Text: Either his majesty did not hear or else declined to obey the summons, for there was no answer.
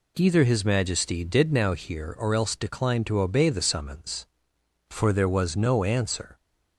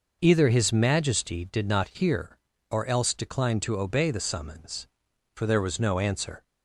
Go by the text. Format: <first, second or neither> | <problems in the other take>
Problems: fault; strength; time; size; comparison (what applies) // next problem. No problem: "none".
second | says "now" for "not"; at 1.5 s